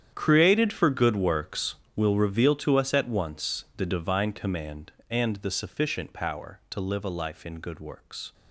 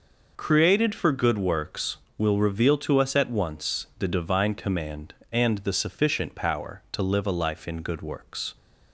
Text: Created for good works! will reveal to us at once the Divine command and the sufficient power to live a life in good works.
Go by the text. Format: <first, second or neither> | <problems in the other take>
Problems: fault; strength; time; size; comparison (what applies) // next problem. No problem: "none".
second | gets quieter; strong; throughout; 16.5 dB